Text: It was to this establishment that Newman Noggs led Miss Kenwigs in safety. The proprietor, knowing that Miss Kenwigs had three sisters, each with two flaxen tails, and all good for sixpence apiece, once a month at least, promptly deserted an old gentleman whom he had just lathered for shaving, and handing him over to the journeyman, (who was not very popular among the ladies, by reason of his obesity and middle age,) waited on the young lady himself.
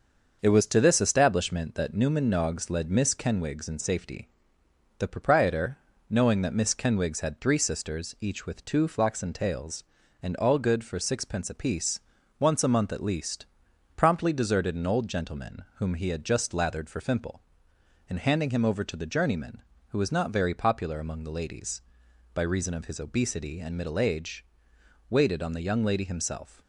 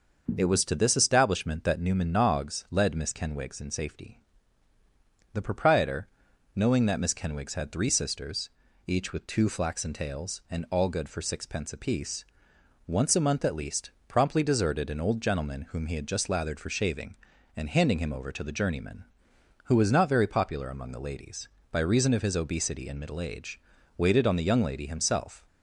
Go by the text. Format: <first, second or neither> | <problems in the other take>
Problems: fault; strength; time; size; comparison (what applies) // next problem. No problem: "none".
second | starts louder than the rest; until 1.4 s; 6 dB; also in the second // says "fimple" for "shaving"; at 17.0 s